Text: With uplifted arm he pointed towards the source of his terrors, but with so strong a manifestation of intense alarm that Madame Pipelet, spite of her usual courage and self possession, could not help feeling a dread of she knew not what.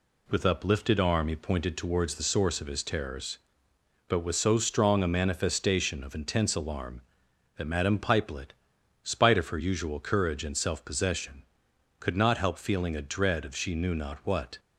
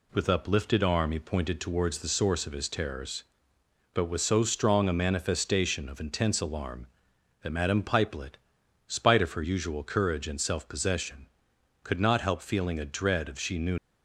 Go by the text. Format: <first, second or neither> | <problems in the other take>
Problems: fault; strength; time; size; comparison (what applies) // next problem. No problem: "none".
first | stops before "not what"; at 13.7 s